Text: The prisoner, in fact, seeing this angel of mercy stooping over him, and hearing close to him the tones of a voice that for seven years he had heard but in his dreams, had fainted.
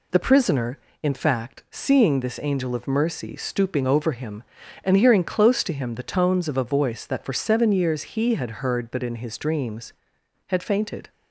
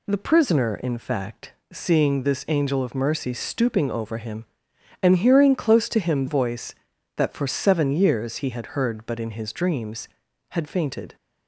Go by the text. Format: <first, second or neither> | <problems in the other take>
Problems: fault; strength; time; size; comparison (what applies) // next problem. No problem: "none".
first | skips "the tones of a"; at 6.2 s